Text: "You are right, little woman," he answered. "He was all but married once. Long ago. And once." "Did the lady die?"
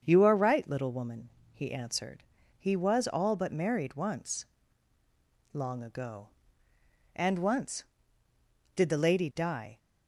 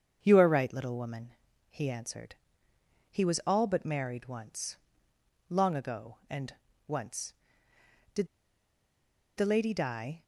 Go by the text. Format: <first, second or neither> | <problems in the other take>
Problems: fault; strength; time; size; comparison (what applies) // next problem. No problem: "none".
first | starts louder than the rest; until 1.2 s; 7 dB; also in the first // pauses between "And" and "once"; slight; at 6.5 s; 0.32 s long // pauses between "Did" and "the"; at 8.2 s; 1.1 s long